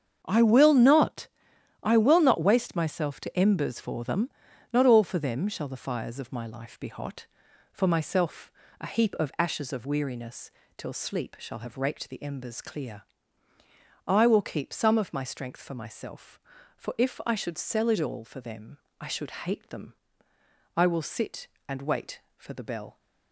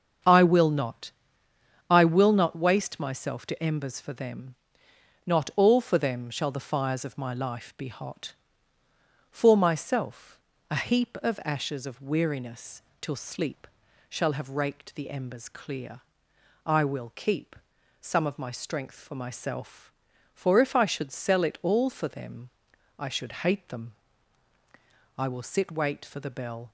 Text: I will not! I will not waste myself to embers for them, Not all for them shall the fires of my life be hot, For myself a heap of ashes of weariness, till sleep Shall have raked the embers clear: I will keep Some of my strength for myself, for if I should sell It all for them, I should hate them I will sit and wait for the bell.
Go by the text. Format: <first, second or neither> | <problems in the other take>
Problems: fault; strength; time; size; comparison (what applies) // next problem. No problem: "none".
first | starts louder than the rest; strong; until 2.0 s; 7.5 dB; strong in the first // pauses between "myself" and "a"; slight; at 10.3 s; 0.32 s long; slight in the first // pauses between "sleep" and "Shall"; at 13.6 s; 0.42 s long // pauses between "keep" and "Some"; at 17.5 s; 0.44 s long // pauses between "them" and "I"; at 23.9 s; 1.2 s long; noticeable in the first // skips "and"; at 25.7 s